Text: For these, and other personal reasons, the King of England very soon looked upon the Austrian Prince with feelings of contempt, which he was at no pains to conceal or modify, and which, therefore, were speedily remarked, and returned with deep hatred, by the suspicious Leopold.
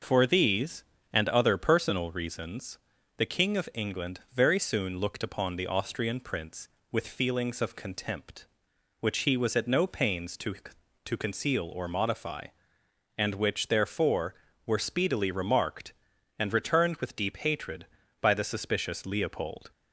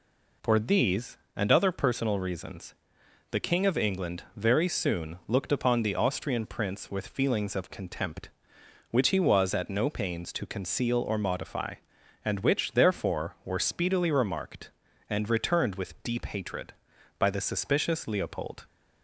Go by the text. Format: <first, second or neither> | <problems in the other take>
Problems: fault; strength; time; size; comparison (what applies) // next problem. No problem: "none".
second | pauses between "England" and "very"; slight; at 4.1 s; 0.16 s long // says "to" twice; at 11.0 s